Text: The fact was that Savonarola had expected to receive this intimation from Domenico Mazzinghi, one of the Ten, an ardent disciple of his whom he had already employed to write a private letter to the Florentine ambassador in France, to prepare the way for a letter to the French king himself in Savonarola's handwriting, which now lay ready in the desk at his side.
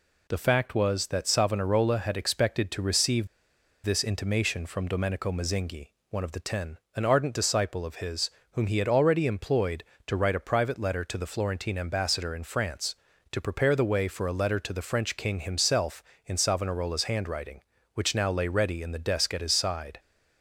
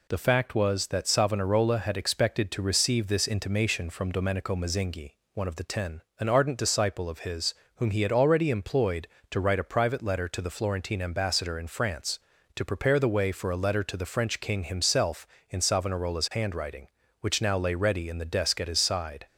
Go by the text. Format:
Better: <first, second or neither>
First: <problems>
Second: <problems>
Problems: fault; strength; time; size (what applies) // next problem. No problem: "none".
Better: second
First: pauses between "receive" and "this"; noticeable; at 3.2 s; 0.56 s long // pauses between "his" and "whom"; slight; at 8.3 s; 0.22 s long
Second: pauses between "his" and "whom"; slight; at 7.5 s; 0.22 s long